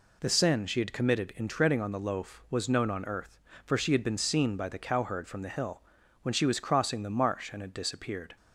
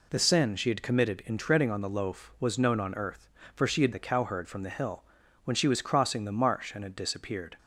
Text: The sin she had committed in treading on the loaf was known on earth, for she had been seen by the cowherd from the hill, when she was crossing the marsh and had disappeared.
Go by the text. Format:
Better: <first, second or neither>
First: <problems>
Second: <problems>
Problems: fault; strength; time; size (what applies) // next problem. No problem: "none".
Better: first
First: none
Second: skips "been seen by"; at 3.9 s